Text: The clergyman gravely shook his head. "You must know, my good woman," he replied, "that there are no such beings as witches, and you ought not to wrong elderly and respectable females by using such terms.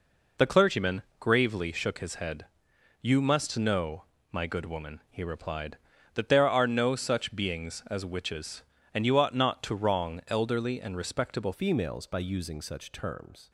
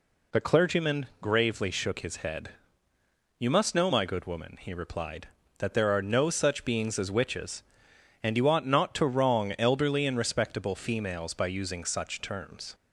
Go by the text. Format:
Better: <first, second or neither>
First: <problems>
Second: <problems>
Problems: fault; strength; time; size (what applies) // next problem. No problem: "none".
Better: second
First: pauses between "clergyman" and "gravely"; slight; at 1.0 s; 0.16 s long // changes voice at "females"; from 11.5 s on; 1.9 s long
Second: none